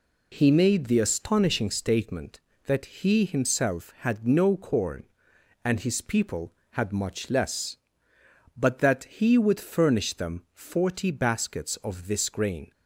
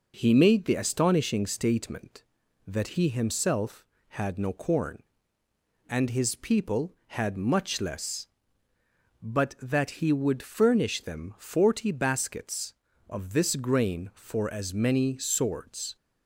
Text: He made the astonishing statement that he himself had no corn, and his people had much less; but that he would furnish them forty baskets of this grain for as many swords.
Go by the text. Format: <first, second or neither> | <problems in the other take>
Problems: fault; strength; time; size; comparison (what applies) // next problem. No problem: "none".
second | stops before "for as many swords"; at 12.7 s